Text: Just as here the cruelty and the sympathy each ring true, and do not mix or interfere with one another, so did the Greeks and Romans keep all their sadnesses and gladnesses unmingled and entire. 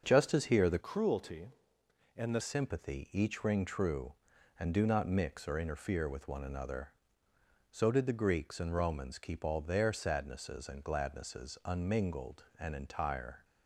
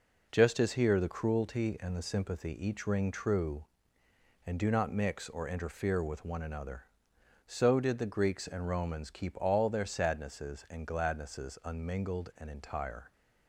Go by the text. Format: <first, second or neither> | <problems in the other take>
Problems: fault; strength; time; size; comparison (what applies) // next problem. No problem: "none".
second | starts louder than the rest; until 1.0 s; 6.5 dB // changes voice from "cruelty" to "the"; from 0.8 to 2.3 s; 1.5 s long